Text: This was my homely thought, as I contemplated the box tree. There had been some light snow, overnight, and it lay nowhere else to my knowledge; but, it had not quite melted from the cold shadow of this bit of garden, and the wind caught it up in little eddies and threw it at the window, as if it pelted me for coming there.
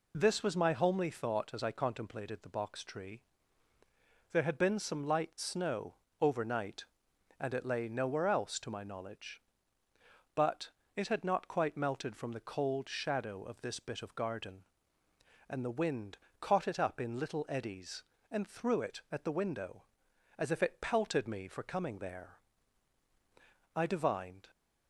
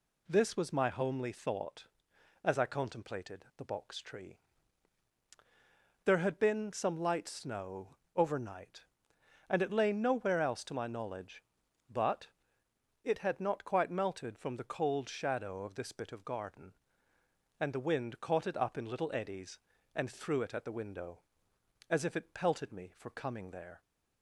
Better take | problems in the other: second | pauses between "wind" and "caught"; slight; at 16.1 s; 0.24 s long // goes on to say "I divined"; noticeable; from 23.7 s on; 0.76 s long

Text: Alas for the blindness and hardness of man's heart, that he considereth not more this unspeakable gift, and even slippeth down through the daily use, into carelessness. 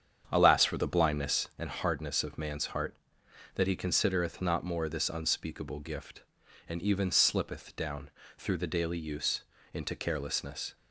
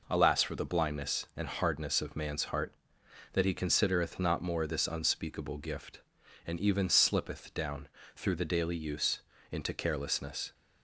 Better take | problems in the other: second | starts louder than the rest; strong; until 1.6 s; 8.5 dB // pauses between "down" and "through"; slight; at 8.0 s; 0.28 s long; slight in the second

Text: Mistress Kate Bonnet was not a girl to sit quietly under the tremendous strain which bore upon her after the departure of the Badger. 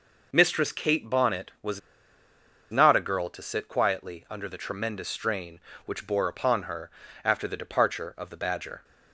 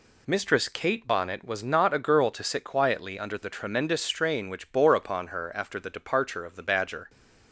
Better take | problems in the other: second | pauses between "was" and "not"; noticeable; at 1.7 s; 0.91 s long // pauses between "her" and "after"; slight; at 6.9 s; 0.32 s long

